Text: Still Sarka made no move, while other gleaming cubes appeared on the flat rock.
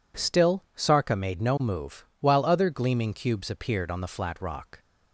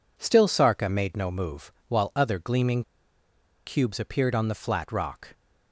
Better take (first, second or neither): first